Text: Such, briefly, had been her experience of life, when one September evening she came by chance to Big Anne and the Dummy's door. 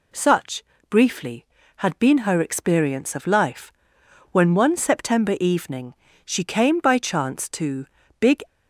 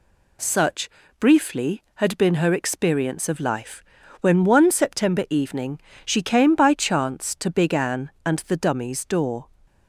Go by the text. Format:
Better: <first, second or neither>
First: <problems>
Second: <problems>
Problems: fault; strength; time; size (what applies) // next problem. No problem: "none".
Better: second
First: pauses between "evening" and "she"; slight; at 5.9 s; 0.30 s long // pauses between "to" and "Big"; slight; at 7.8 s; 0.31 s long // stops before "Anne and the Dummy's door"; at 8.4 s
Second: pauses between "evening" and "she"; slight; at 5.7 s; 0.28 s long